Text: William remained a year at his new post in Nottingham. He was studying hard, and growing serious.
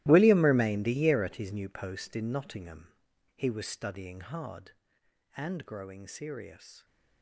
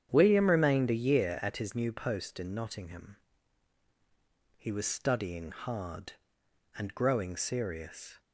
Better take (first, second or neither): second